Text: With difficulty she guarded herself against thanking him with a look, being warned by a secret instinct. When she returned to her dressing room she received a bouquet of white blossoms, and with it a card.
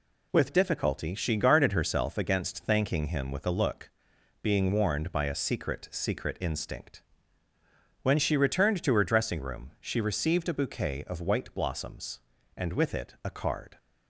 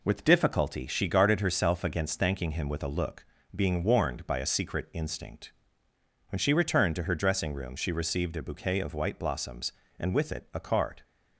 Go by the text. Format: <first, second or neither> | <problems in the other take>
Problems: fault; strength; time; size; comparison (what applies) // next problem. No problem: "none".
second | says "secret" twice; at 5.8 s